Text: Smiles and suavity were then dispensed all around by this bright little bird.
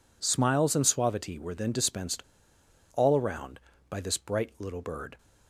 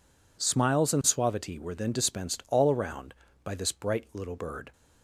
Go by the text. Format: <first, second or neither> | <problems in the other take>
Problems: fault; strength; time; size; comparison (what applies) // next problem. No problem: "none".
second | pauses between "dispensed" and "all"; noticeable; at 2.2 s; 0.71 s long